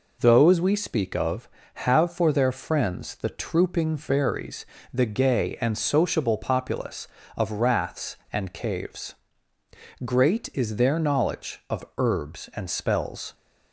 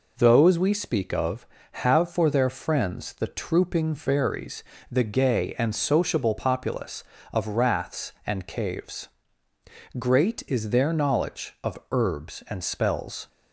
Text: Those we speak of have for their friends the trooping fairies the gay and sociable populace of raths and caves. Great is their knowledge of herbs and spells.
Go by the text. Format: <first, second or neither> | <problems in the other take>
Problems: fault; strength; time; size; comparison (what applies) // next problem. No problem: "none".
neither | pauses between "fairies" and "the"; slight; the same in both